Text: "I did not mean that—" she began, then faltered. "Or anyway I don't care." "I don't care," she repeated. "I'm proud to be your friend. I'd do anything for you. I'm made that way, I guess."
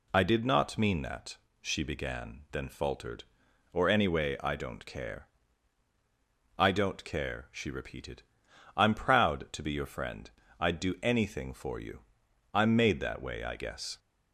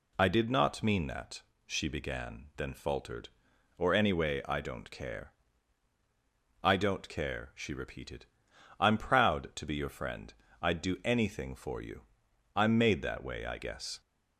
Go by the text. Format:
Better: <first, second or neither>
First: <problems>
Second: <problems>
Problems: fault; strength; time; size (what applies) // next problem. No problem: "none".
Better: neither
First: none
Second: none